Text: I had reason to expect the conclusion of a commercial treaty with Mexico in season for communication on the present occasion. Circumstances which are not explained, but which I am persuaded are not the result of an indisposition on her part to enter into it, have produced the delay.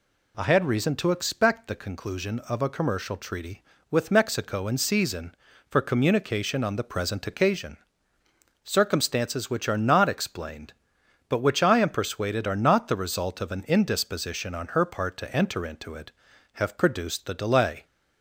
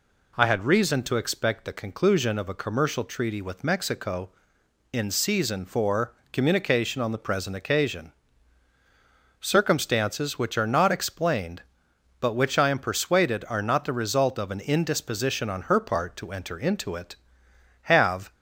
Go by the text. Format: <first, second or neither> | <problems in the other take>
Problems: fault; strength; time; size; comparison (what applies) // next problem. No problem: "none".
first | pauses between "for" and "communication"; slight; at 6.1 s; 0.20 s long // stops before "produced the delay"; at 18.3 s